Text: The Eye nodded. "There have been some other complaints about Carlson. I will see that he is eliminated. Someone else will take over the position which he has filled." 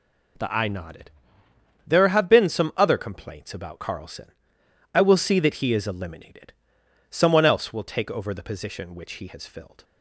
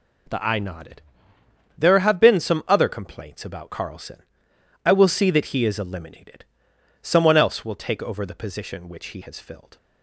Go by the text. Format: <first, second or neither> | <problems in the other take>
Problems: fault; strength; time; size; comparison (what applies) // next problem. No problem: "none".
neither | none